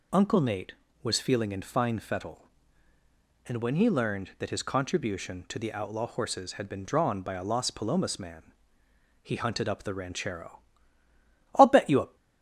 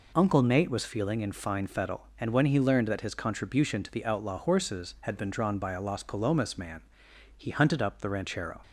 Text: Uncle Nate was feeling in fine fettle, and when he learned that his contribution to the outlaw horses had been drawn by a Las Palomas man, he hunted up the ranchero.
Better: second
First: goes on to say "I'll bet you a"; from 11.5 s on; 0.60 s long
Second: none

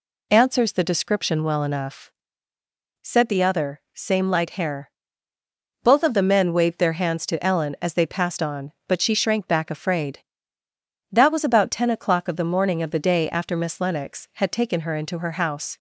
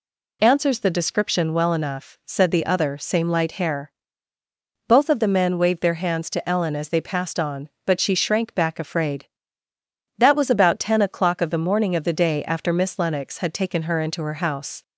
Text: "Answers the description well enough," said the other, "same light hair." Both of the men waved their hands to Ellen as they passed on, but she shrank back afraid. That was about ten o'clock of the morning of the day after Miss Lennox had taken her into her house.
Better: neither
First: none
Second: none

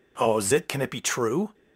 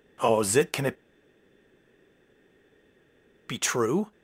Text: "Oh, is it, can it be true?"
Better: first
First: none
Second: pauses between "it" and "be"; strong; at 0.9 s; 2.5 s long

